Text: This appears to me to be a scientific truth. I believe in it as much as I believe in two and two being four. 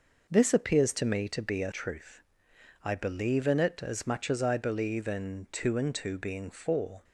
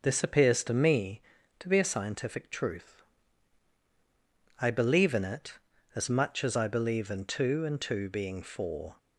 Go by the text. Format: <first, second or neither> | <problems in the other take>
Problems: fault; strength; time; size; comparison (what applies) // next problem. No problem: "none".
second | skips "scientific"; at 1.7 s